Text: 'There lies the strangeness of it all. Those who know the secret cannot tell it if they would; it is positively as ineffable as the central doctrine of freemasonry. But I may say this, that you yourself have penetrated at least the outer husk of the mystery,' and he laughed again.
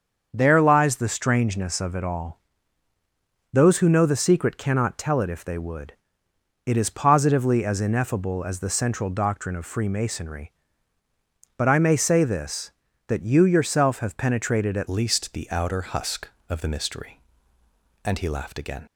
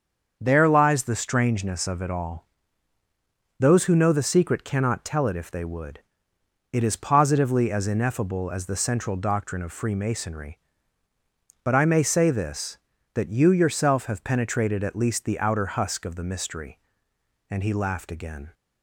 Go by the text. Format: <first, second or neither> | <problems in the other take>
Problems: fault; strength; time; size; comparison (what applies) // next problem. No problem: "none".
second | starts louder than the rest; until 1.3 s; 7 dB; also in the second // changes voice at "least"; from 14.8 s on; 4.0 s long